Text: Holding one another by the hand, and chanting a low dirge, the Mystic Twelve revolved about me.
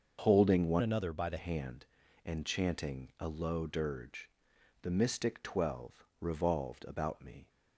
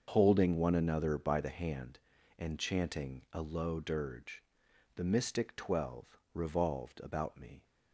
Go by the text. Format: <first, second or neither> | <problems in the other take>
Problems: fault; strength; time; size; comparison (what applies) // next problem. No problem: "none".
second | starts louder than the rest; until 1.2 s; 6.5 dB; also in the second // changes voice from "another" to "the"; from 0.8 to 1.3 s; 0.5 s long // pauses between "Twelve" and "revolved"; slight; at 6.0 s; 0.16 s long; slight in the second